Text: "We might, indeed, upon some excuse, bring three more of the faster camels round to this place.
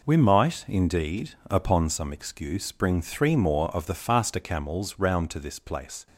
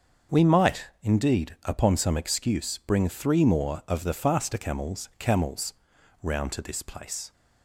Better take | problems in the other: first | starts louder than the rest; until 1.4 s; 6.5 dB // says "camels" twice; at 5.1 s

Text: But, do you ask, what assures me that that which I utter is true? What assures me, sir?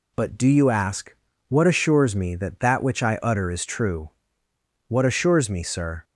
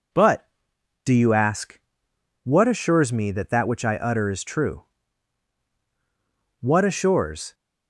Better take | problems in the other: first | stops before "me sir"; at 7.5 s

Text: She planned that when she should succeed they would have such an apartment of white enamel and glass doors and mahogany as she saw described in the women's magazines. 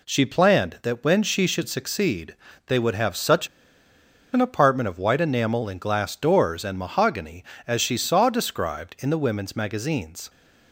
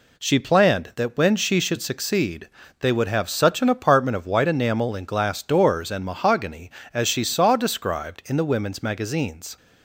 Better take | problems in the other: second | pauses between "succeed" and "they"; slight; at 2.3 s; 0.32 s long; slight in the second // pauses between "such" and "an"; noticeable; at 3.4 s; 0.85 s long

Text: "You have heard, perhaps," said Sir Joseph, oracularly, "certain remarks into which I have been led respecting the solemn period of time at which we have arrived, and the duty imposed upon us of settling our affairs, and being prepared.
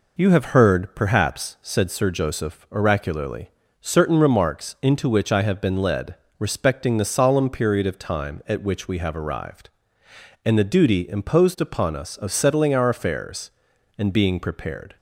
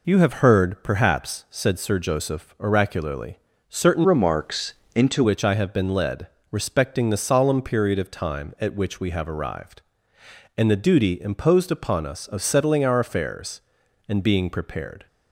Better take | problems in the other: first | changes voice from "remarks" to "into"; from 4.0 to 5.2 s; 1.2 s long // pauses between "remarks" and "into"; slight; at 4.7 s; 0.22 s long // pauses between "led" and "respecting"; slight; at 6.2 s; 0.24 s long; slight in the first

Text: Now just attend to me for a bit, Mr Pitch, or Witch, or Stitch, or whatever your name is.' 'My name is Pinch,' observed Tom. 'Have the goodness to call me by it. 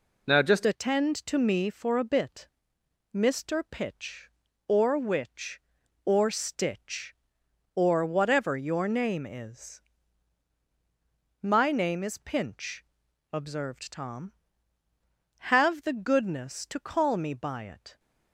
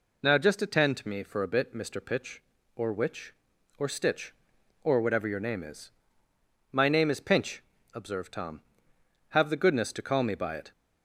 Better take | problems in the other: second | changes voice at "attend"; from 0.6 s on; 17.3 s long

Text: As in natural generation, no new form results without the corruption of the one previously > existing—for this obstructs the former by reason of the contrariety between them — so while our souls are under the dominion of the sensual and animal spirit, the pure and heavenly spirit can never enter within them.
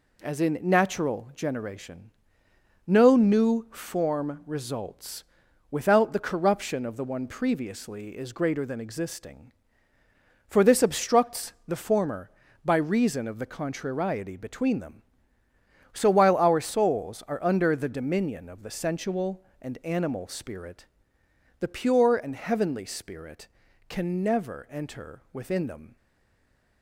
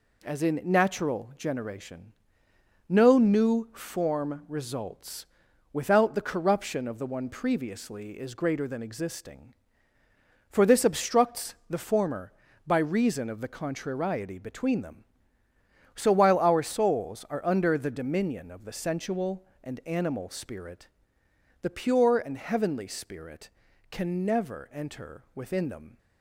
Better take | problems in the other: second | pauses between "results" and "without"; noticeable; at 5.2 s; 0.48 s long; noticeable in the second // stays silent after the last word; slight; from 25.9 s on; 0.9 s long

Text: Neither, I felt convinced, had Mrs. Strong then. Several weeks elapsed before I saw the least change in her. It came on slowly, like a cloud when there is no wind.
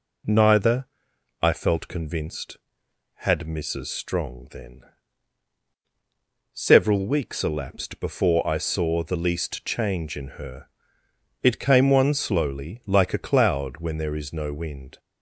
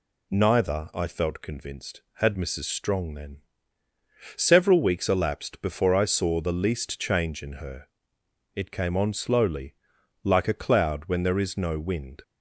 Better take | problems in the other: second | says "one" for "on"; at 11.9 s

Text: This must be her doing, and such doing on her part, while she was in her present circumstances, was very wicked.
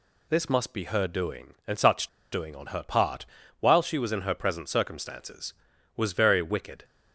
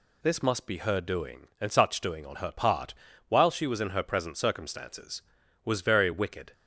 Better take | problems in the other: second | pauses between "such" and "doing"; slight; at 2.0 s; 0.24 s long

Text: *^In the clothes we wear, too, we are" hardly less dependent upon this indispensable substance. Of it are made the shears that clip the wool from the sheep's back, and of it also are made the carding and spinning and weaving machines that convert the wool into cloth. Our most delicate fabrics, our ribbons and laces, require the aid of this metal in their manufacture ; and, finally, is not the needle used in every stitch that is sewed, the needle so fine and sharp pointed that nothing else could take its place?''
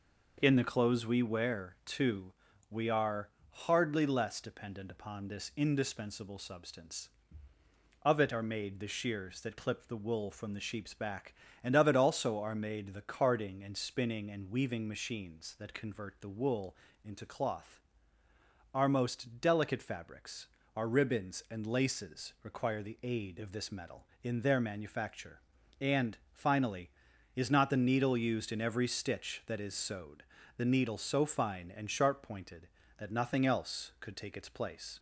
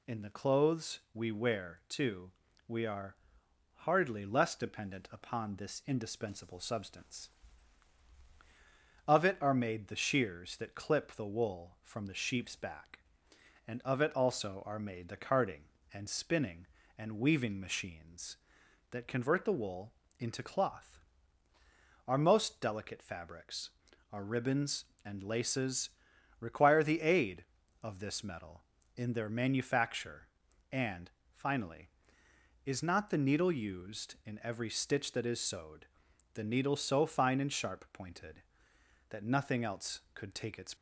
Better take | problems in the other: first | pauses between "are" and "hardly"; noticeable; at 3.1 s; 0.56 s long; slight in the first // pauses between "wool" and "into"; slight; at 19.9 s; 0.24 s long; slight in the first // stops before "place"; at 40.7 s

